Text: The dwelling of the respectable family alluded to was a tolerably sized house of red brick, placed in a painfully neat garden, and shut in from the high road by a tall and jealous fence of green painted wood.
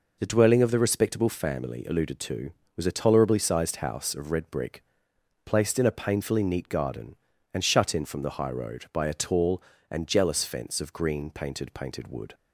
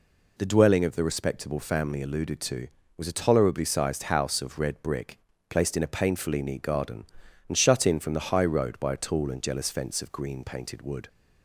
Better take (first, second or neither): second